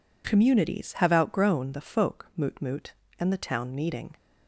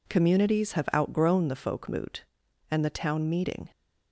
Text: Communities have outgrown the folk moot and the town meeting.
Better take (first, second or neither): second